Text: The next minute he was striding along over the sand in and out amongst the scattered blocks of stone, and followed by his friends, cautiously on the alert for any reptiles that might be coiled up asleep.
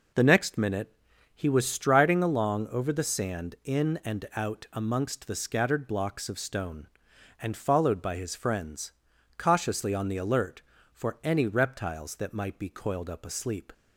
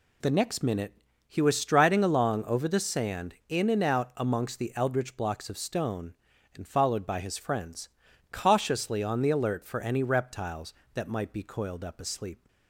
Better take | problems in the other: first | pauses between "minute" and "he"; slight; at 0.9 s; 0.34 s long; also in the first // says "eldritch" for "scattered"; at 4.7 s

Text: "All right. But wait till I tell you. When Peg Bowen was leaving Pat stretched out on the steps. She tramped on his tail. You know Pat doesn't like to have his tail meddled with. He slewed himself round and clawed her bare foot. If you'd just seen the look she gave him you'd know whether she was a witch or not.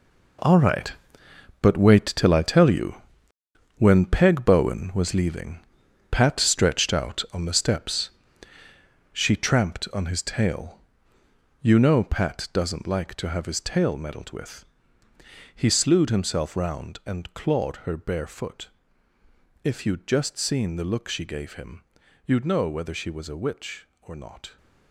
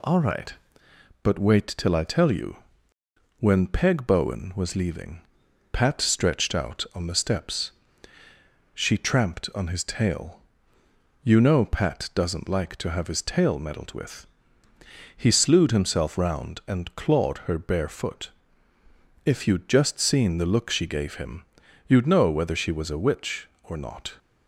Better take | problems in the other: second | gets quieter; strong; throughout; 12 dB // pauses between "leaving" and "Pat"; noticeable; at 5.5 s; 0.50 s long; noticeable in the second // pauses between "him" and "you'd"; at 21.8 s; 0.44 s long; also in the second

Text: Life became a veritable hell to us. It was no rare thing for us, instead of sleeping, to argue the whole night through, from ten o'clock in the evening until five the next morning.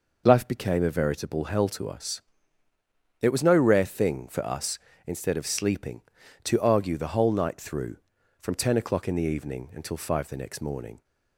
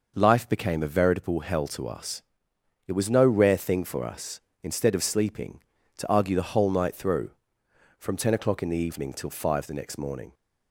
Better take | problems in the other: first | says "till" for "until"; at 9.1 s

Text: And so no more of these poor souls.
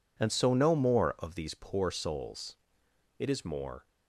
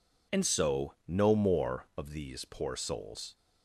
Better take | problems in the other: second | goes on to say "It is more"; noticeable; from 3.1 s on; 0.70 s long

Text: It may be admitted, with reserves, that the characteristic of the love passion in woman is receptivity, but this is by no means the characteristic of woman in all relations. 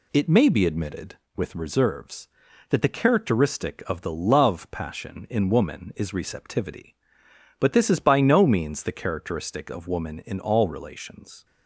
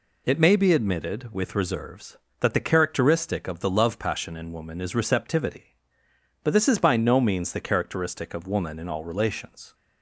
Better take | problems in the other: neither | none

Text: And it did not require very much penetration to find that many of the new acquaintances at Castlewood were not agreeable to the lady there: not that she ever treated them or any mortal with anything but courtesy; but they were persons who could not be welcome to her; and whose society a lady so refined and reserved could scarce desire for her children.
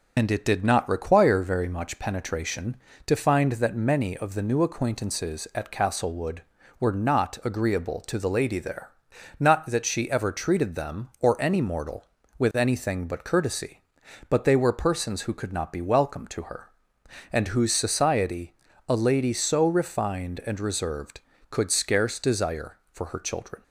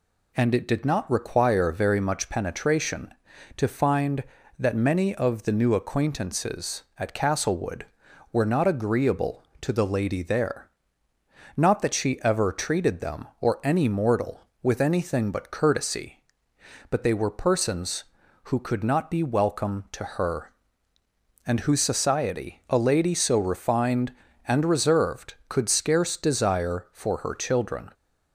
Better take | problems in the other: second | loses the start of "And"; at 0.1 s; 50 ms // pauses between "society" and "a"; slight; at 18.5 s; 0.36 s long

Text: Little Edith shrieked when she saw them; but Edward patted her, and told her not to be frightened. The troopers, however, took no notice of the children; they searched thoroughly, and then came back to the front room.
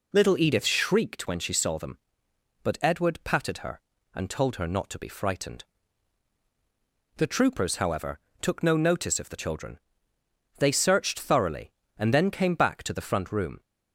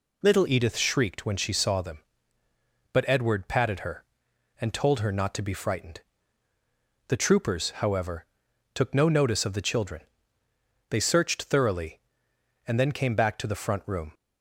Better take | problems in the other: first | changes voice at "Edith"; from 0.4 s on; 13.7 s long

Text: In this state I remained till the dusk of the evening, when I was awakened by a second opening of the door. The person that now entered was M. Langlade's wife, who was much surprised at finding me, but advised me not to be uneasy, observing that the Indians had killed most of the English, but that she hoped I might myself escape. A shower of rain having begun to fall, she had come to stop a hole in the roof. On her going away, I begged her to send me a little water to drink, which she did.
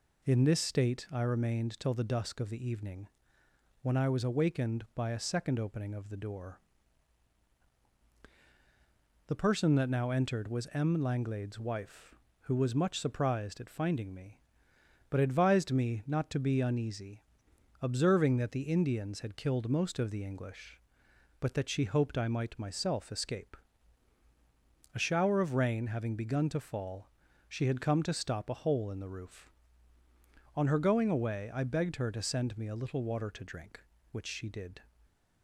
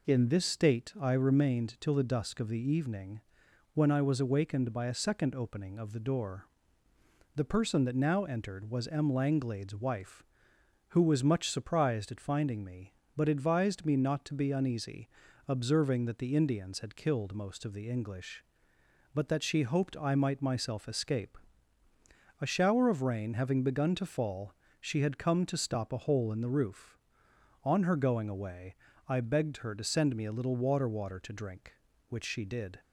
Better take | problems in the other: first | says "water" twice; at 30.8 s

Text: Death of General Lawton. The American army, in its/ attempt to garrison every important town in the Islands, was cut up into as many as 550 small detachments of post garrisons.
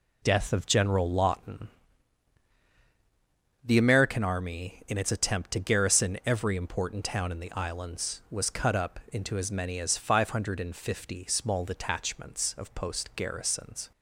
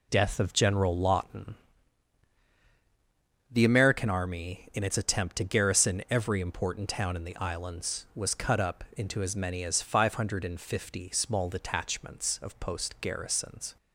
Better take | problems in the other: neither | none

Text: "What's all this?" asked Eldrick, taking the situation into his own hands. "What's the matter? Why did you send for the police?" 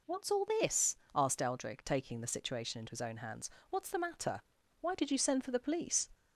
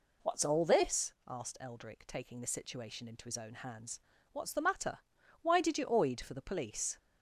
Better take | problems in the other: first | says "oid" for "send"; at 5.8 s

